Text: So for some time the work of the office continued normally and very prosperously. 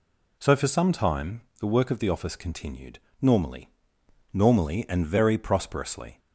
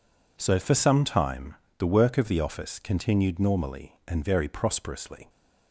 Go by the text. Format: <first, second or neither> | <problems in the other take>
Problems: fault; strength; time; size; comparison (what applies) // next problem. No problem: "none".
second | pauses between "time" and "the"; slight; at 1.4 s; 0.18 s long; slight in the second // pauses between "continued" and "normally"; slight; at 2.9 s; 0.20 s long // says "normally" twice; at 4.3 s